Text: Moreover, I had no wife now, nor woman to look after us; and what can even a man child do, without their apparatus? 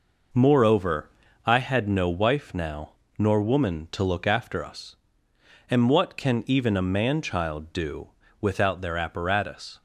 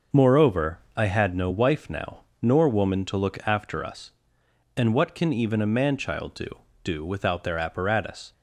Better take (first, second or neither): first